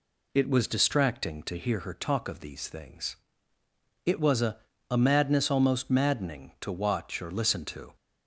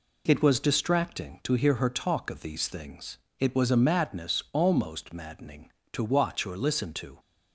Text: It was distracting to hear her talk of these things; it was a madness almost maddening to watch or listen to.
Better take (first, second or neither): second